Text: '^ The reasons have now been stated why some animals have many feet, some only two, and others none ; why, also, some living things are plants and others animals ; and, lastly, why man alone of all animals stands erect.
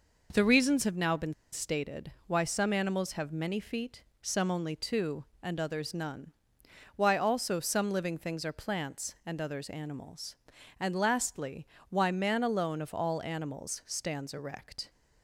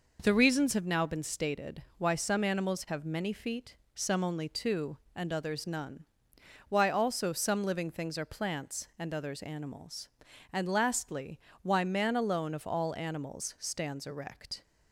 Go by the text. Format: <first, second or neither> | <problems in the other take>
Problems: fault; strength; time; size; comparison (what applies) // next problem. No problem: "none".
second | pauses between "been" and "stated"; slight; at 1.3 s; 0.19 s long // pauses between "stated" and "why"; slight; at 2.0 s; 0.16 s long; slight in the second